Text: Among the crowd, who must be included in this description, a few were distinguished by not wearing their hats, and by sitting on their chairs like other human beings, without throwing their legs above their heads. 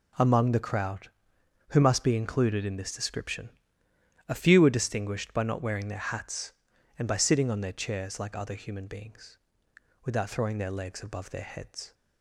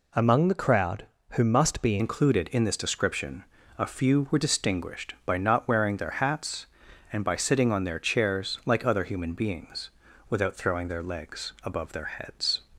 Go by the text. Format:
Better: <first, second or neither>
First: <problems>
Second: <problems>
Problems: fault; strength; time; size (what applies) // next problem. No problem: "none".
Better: first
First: none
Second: changes voice at "included"; from 1.9 s on; 10.7 s long